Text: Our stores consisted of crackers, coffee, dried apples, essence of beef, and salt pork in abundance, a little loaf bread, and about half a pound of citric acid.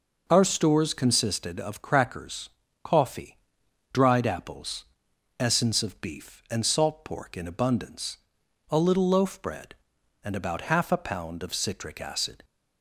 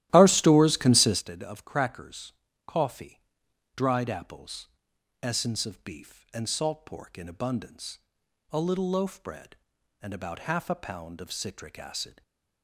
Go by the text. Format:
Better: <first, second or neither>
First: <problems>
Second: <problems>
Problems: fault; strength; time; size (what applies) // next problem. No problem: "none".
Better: first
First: none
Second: starts louder than the rest; strong; until 1.2 s; 14 dB // stays silent after the last word; slight; from 12.1 s on; 0.5 s long